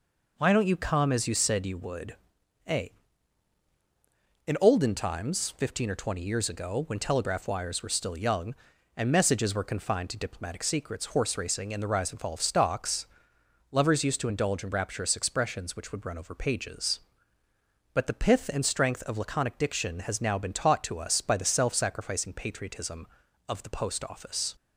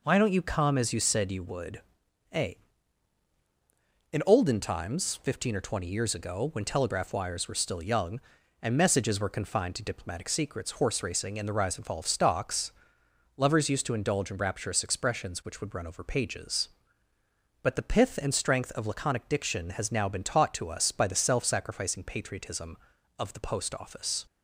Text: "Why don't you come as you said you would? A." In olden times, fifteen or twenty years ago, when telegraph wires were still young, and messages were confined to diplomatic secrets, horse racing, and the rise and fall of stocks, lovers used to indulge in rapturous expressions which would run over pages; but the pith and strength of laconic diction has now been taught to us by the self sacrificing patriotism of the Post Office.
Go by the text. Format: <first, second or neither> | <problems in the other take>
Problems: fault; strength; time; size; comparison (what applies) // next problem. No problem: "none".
neither | none